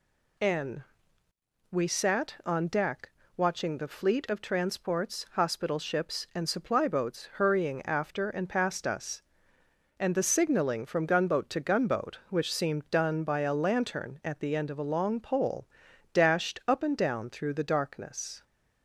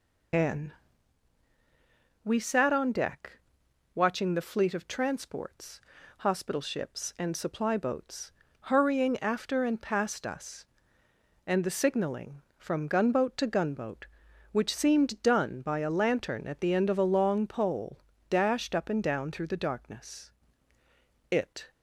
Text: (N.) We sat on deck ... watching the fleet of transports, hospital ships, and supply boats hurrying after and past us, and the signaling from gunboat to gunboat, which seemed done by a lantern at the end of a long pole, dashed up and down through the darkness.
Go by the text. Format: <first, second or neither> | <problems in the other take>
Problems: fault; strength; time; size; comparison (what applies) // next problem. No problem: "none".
first | pauses between "boats" and "hurrying"; slight; at 8.3 s; 0.30 s long // goes on to say "It"; slight; from 21.3 s on; 0.40 s long